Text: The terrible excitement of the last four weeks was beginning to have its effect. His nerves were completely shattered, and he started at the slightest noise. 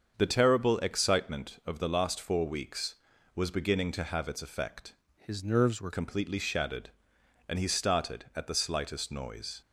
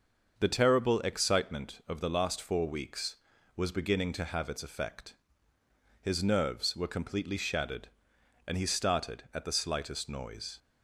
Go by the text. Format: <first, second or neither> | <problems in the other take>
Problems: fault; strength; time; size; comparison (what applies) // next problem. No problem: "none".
second | starts louder than the rest; until 1.1 s; 7 dB; also in the second // changes voice from "His" to "were"; from 5.1 to 5.9 s; 0.8 s long